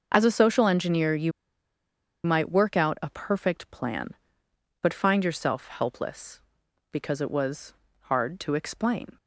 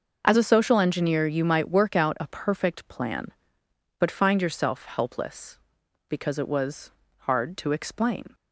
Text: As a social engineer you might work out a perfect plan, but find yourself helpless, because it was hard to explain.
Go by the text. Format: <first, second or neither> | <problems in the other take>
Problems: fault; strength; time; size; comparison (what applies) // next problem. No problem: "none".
second | pauses between "you" and "might"; noticeable; at 1.3 s; 0.95 s long // pauses between "was" and "hard"; slight; at 7.7 s; 0.28 s long; slight in the second